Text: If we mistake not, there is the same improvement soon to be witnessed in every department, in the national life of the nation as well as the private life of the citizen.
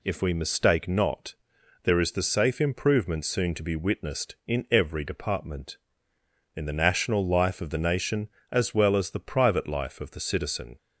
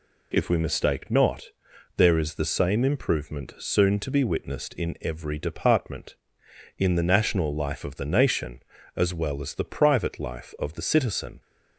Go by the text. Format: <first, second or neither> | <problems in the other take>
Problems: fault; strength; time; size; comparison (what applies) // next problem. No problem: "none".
second | says "safe" for "same"; at 2.2 s